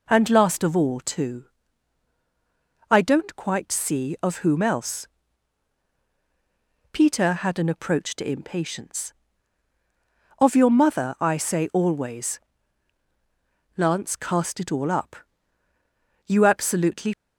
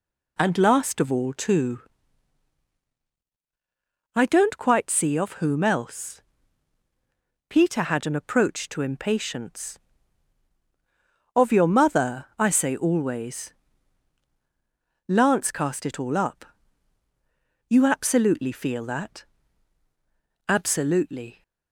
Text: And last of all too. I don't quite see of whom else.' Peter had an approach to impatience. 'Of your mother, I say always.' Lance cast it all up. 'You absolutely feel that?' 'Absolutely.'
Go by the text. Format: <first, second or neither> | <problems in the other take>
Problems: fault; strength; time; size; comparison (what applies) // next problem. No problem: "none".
second | stops before "feel that Absolutely"; at 17.1 s